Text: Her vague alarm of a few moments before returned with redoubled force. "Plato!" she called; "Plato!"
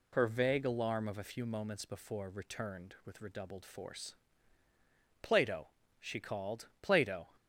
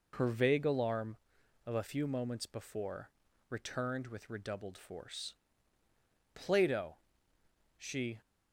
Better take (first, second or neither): first